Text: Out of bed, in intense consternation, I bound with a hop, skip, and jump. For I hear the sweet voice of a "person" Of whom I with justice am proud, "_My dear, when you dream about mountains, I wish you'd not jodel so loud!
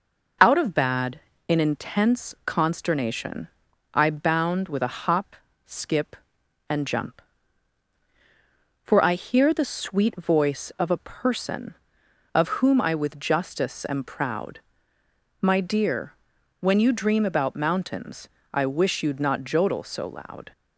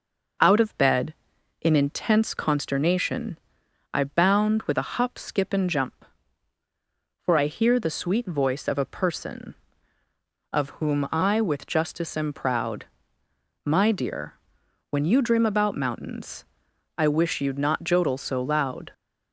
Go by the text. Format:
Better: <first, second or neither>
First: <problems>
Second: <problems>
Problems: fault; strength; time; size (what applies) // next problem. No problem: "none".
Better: second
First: says "bad" for "bed"; at 0.7 s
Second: none